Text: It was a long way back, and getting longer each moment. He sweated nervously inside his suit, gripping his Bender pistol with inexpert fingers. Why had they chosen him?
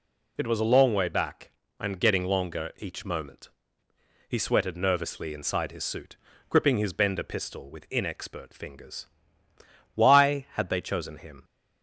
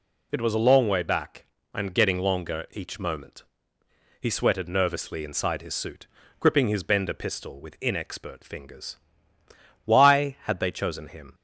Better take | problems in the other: neither | none

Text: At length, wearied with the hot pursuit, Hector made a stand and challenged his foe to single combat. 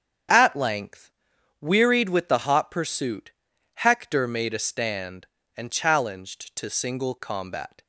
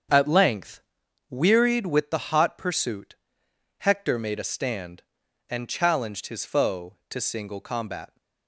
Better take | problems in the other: second | starts louder than the rest; strong; until 1.8 s; 8 dB; strong in the second // skips "his foe"; at 6.5 s

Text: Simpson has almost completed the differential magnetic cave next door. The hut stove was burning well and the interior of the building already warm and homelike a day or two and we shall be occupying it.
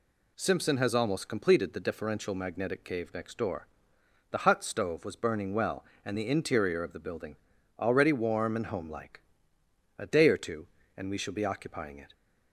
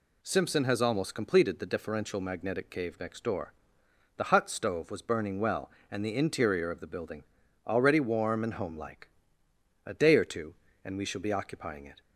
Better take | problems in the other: neither | pauses between "building" and "already"; the same in both // pauses between "homelike" and "a"; noticeable; the same in both

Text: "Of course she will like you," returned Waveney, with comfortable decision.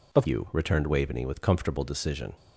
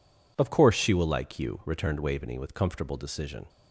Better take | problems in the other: second | skips "course she will like"; at 0.2 s

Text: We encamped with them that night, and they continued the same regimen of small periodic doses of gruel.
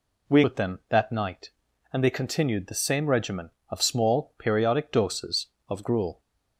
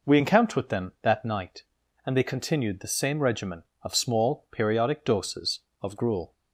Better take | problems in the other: second | skips "encamped"; at 0.4 s

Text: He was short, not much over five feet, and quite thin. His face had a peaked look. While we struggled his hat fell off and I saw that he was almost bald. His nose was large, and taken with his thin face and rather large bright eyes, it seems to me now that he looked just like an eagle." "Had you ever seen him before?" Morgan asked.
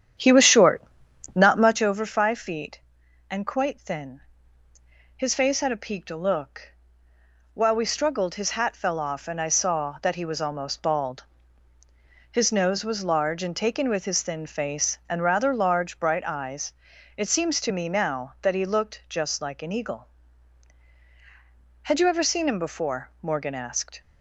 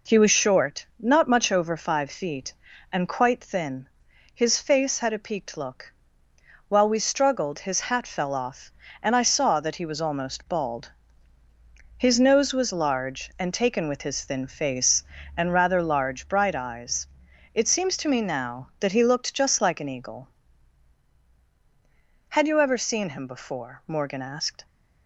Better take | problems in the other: second | starts louder than the rest; strong; until 1.9 s; 9.5 dB

